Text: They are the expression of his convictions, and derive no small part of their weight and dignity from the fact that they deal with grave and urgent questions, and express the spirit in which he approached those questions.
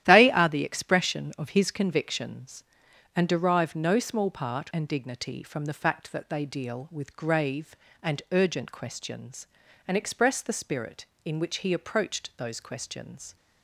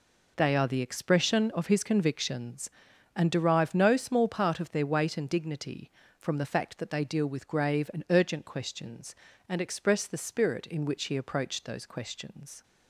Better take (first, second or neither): second